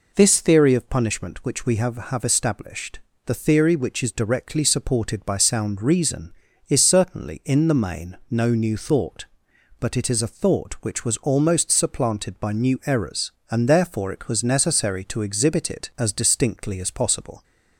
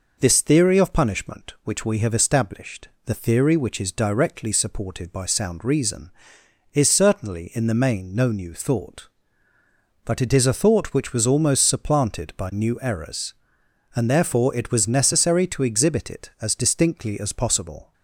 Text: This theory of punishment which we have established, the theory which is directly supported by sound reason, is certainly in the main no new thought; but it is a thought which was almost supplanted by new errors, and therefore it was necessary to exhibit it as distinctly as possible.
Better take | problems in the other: second | says "have" twice; at 2.0 s

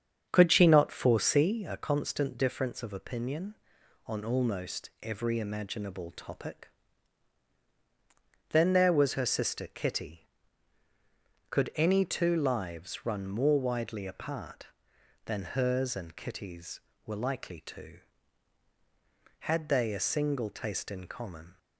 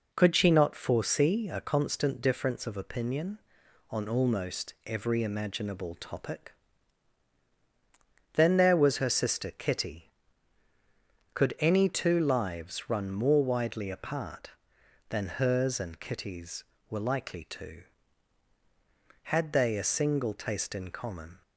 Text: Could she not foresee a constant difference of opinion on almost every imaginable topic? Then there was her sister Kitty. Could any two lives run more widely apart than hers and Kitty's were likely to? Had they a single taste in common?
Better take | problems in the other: second | starts louder than the rest; strong; until 1.5 s; 7.5 dB

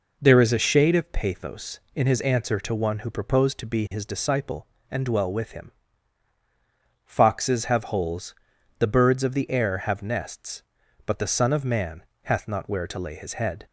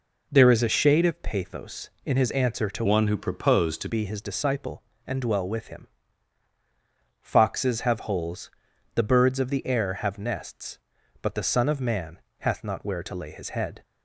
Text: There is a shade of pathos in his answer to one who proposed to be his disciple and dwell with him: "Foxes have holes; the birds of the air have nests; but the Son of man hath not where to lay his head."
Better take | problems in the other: first | changes voice from "one" to "to"; from 2.8 to 3.8 s; 1.0 s long // pauses between "man" and "hath"; slight; at 12.1 s; 0.22 s long; slight in the first

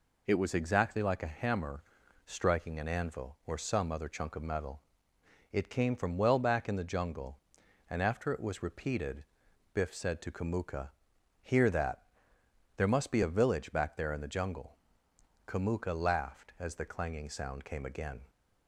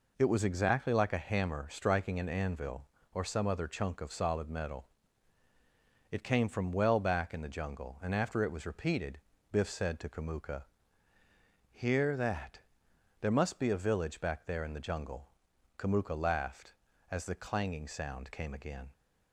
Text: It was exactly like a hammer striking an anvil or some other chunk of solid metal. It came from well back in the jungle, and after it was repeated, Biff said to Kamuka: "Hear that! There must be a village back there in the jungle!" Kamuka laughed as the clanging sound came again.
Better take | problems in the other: second | pauses between "hammer" and "striking"; at 1.8 s; 0.44 s long // skips "solid"; at 4.4 s

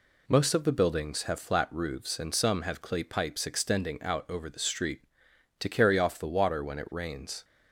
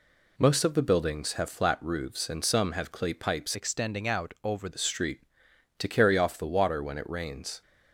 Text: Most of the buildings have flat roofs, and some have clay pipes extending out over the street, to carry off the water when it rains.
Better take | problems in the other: first | changes voice from "extending" to "over"; from 3.5 to 4.6 s; 1.1 s long

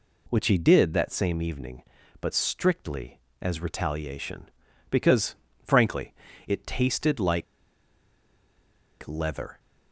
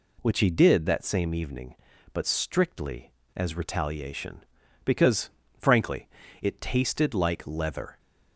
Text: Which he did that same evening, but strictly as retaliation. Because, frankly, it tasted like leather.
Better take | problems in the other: second | pauses between "like" and "leather"; strong; at 7.4 s; 1.6 s long

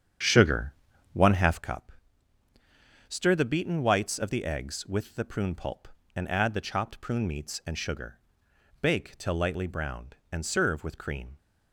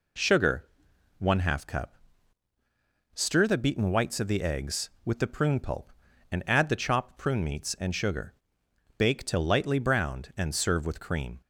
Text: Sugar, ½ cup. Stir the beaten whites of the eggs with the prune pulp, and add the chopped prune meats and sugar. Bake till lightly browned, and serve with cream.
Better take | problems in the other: second | starts louder than the rest; strong; until 1.6 s; 8.5 dB

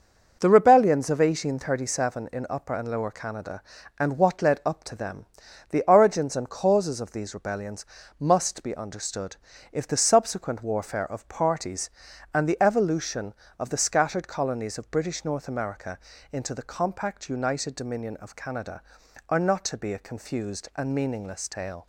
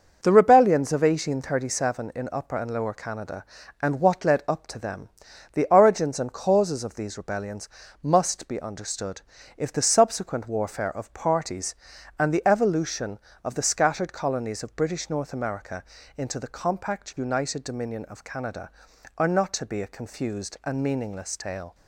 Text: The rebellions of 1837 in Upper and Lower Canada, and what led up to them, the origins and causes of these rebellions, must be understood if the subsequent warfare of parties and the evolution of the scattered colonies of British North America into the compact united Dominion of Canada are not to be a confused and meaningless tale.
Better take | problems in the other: neither | pauses between "understood" and "if"; slight; the same in both // pauses between "America" and "into"; slight; the same in both

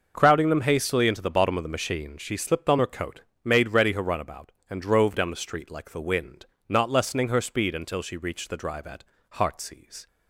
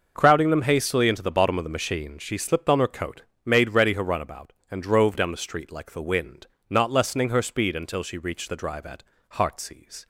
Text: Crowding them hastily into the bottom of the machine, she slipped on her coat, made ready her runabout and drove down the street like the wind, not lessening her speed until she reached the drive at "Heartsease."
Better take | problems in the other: neither | pauses between "at" and "Heartsease"; slight; the same in both

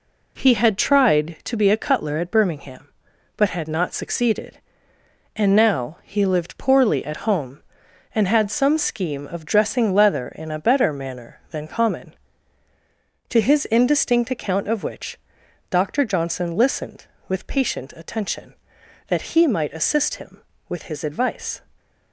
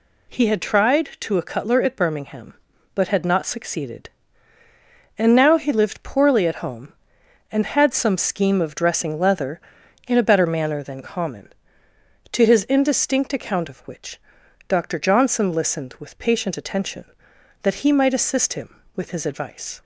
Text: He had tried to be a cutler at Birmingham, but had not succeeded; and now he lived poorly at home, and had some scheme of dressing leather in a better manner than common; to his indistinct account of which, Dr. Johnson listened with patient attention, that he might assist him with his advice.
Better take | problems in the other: first | skips "be"; at 1.3 s

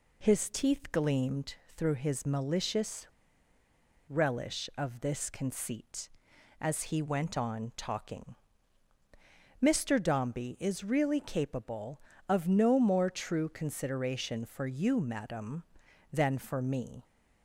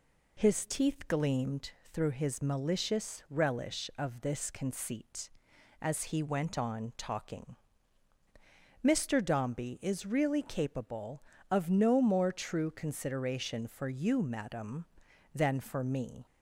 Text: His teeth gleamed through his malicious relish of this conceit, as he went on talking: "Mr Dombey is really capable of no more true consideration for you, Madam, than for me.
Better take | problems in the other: second | pauses between "gleamed" and "through"; slight; at 1.5 s; 0.20 s long; slight in the second // pauses between "malicious" and "relish"; at 3.0 s; 0.99 s long

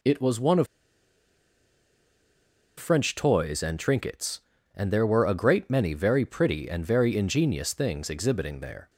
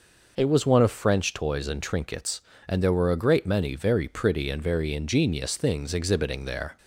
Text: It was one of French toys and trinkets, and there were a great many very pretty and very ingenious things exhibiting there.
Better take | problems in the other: second | pauses between "of" and "French"; strong; at 0.6 s; 2.1 s long

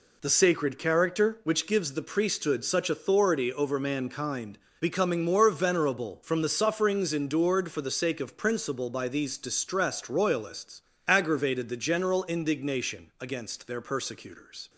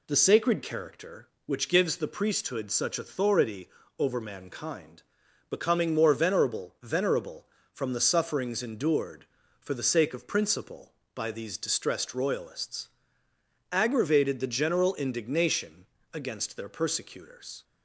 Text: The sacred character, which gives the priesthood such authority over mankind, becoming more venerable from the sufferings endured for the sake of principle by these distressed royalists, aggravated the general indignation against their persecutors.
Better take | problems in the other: first | pauses between "authority" and "over"; slight; at 3.6 s; 0.28 s long // says "venerable" twice; at 6.8 s // pauses between "indignation" and "against"; slight; at 15.8 s; 0.26 s long

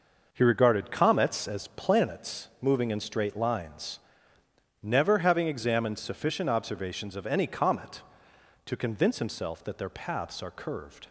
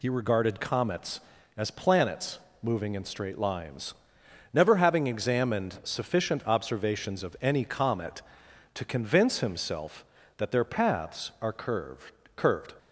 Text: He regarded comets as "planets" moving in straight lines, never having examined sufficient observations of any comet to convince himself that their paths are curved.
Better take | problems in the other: first | pauses between "planets" and "moving"; slight; at 2.3 s; 0.20 s long // says "curved" twice; at 12.3 s

